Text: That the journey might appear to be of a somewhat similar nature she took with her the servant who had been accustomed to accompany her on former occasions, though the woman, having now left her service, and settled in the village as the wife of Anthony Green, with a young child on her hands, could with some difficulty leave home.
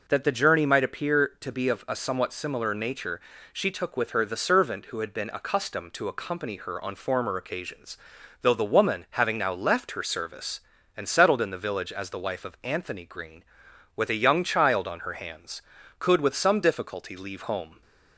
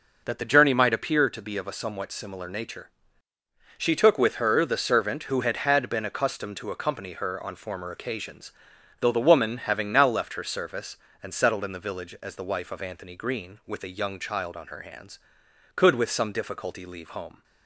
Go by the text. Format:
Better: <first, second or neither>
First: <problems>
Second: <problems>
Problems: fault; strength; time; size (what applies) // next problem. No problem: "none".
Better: first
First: pauses between "nature" and "she"; slight; at 3.1 s; 0.32 s long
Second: pauses between "nature" and "she"; noticeable; at 2.8 s; 0.88 s long // says "had" twice; at 5.5 s